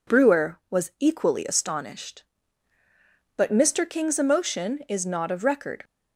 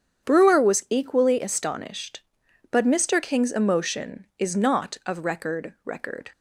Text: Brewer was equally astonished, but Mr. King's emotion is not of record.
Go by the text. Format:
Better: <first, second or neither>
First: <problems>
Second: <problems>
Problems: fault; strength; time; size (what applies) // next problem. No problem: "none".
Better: first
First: none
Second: starts louder than the rest; strong; until 1.3 s; 8.5 dB // says "record" twice; at 5.8 s